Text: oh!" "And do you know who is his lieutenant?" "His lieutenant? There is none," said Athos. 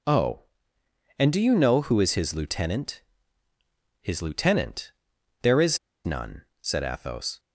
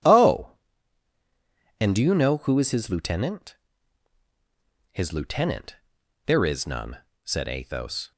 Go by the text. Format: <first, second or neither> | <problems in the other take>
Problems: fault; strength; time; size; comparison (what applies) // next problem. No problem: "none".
second | pauses between "is" and "none"; slight; at 5.7 s; 0.26 s long